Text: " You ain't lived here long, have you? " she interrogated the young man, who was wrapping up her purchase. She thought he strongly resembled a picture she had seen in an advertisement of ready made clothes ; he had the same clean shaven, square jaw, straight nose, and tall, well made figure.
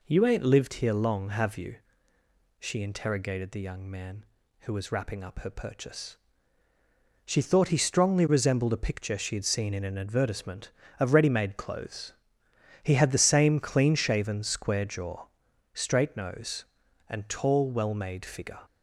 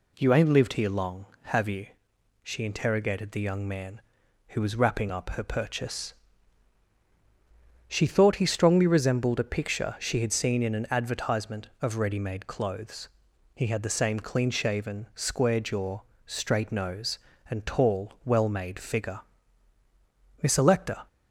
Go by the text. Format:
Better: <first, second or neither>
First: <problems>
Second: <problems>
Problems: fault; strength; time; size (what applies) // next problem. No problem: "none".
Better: first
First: none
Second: goes on to say "Miss Electa"; noticeable; from 20.4 s on; 0.64 s long